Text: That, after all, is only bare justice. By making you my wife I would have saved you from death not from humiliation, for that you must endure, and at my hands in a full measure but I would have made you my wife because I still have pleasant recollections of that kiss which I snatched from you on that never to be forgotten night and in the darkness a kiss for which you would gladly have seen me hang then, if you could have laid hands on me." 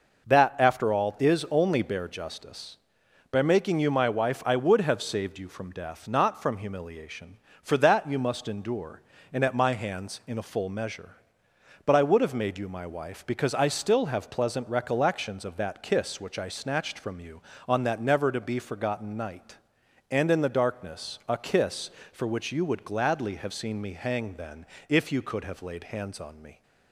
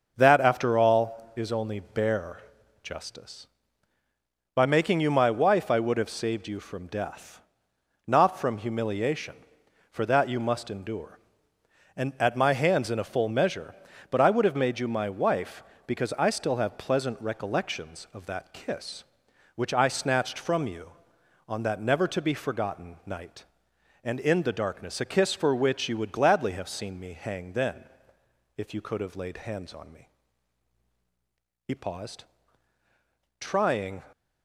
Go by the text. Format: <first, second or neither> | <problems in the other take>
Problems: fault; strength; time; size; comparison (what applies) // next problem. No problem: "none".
first | starts louder than the rest; noticeable; until 1.1 s; 6 dB // pauses between "bare" and "justice"; at 2.4 s; 0.42 s long // pauses between "death" and "not"; noticeable; at 7.3 s; 0.66 s long // goes on to say "He paused trying"; strong; from 31.6 s on; 2.3 s long